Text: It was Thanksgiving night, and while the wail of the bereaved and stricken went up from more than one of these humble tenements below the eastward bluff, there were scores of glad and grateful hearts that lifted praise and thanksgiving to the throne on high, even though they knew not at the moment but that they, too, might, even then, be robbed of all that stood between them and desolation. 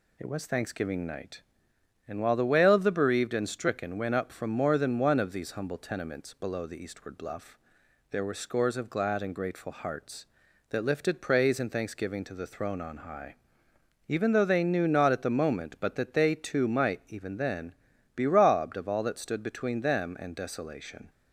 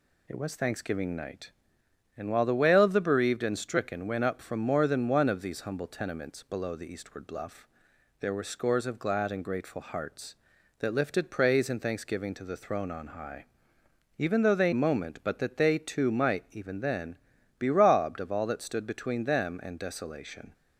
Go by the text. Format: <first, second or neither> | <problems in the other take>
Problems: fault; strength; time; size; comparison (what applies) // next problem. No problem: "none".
first | skips "knew not at the"; at 14.7 s